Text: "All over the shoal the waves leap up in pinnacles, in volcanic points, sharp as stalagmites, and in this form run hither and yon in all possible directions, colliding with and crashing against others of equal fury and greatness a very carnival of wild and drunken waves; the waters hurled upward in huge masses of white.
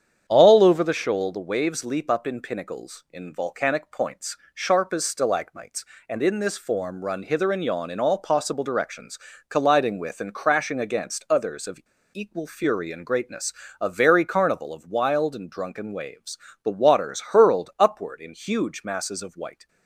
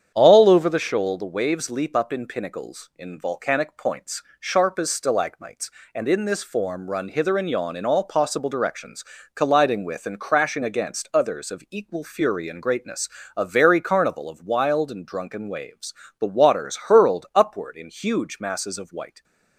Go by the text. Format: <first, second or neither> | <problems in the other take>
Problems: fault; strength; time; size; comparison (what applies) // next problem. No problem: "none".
second | starts louder than the rest; strong; until 1.2 s; 8.5 dB; strong in the second // pauses between "of" and "equal"; slight; at 11.8 s; 0.32 s long // pauses between "greatness" and "a"; slight; at 13.5 s; 0.26 s long; slight in the second